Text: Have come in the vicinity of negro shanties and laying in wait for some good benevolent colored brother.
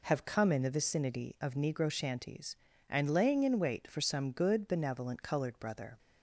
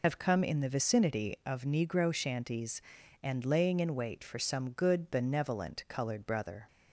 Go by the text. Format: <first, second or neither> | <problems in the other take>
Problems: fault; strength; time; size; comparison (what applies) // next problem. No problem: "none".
first | loses the start of "Have"; at 0.0 s; 75 ms